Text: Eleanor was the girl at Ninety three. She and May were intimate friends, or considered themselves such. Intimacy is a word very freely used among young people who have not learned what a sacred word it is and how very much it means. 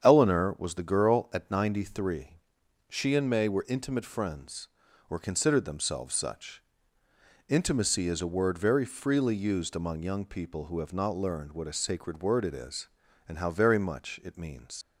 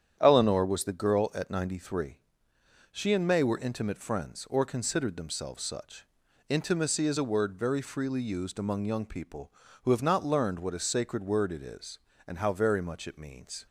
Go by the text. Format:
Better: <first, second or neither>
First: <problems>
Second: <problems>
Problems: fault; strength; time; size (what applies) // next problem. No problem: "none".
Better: second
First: starts louder than the rest; strong; until 1.0 s; 8 dB // leaves "means" unfinished; at 14.8 s; 80 ms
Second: starts louder than the rest; strong; until 1.2 s; 9.5 dB